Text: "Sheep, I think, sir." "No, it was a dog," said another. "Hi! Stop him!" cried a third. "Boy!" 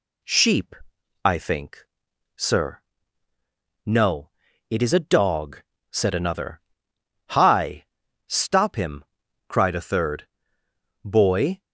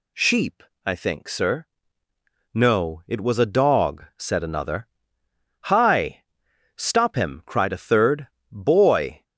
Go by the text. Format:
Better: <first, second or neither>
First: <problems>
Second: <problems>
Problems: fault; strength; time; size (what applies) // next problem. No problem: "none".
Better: second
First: says "is" for "was"; at 4.8 s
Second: none